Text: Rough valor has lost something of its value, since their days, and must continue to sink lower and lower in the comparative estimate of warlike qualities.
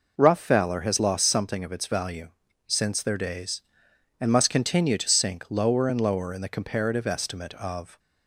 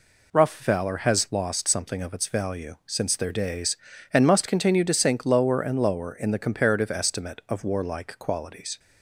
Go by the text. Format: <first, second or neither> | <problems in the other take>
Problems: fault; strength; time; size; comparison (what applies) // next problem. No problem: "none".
second | stops before "warlike qualities"; at 7.9 s